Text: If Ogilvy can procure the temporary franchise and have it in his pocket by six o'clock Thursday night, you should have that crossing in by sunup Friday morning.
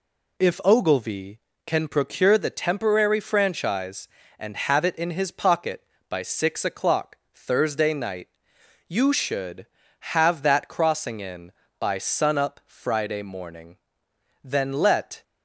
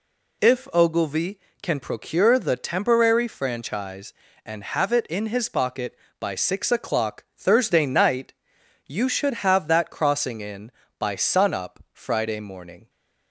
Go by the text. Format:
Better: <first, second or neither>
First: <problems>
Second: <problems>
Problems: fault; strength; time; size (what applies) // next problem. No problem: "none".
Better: second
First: pauses between "o'clock" and "Thursday"; slight; at 7.1 s; 0.16 s long // goes on to say "Then let"; noticeable; from 14.4 s on; 0.78 s long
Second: none